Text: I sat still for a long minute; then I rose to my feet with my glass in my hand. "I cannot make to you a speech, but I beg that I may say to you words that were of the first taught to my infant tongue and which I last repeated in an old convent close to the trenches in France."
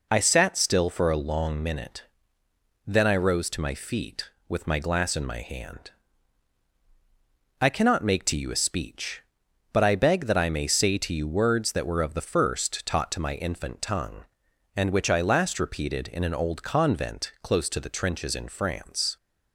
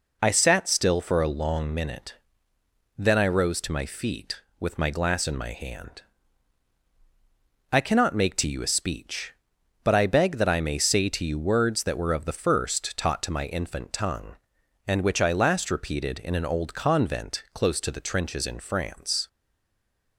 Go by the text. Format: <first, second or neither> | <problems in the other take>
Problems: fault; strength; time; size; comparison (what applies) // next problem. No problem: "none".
first | stays silent after the last word; slight; from 19.2 s on; 0.9 s long